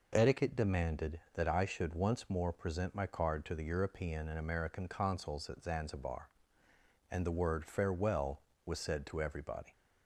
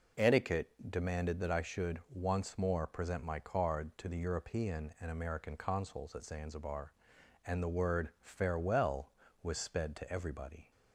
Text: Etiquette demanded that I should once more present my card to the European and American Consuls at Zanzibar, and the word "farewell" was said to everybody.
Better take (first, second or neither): first